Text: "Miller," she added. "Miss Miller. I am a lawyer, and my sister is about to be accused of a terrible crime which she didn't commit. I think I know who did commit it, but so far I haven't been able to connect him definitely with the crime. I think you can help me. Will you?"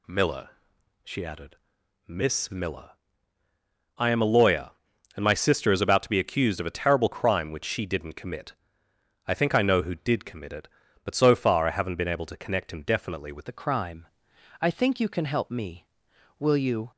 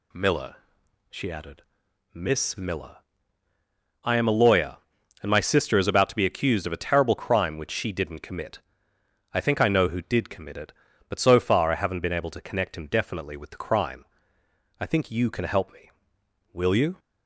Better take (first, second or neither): second